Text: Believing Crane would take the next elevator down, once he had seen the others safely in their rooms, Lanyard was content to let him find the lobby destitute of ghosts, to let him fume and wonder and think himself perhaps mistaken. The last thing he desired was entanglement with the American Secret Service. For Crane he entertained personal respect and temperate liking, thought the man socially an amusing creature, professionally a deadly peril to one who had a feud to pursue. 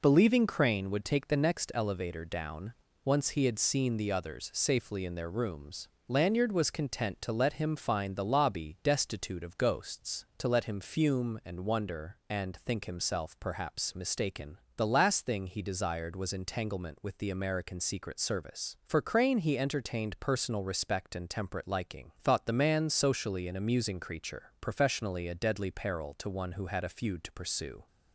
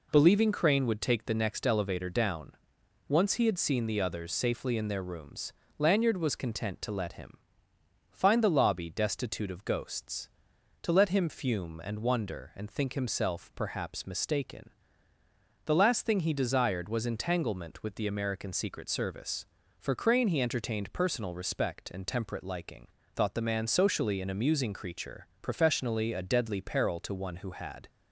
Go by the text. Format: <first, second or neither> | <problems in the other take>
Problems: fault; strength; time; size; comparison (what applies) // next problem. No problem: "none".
first | pauses between "him" and "find"; noticeable; at 7.3 s; 0.76 s long // stops before "a feud to pursue"; at 27.8 s